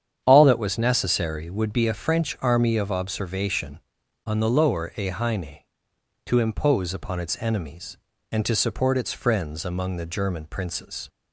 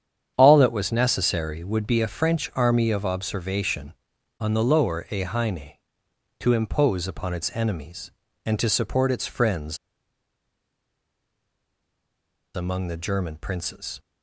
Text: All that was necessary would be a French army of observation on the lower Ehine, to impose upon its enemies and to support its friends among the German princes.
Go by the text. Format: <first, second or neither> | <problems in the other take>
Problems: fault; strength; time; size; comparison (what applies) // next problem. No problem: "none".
first | starts louder than the rest; strong; until 1.3 s; 8.5 dB; strong in the first // pauses between "friends" and "among"; strong; at 9.7 s; 2.7 s long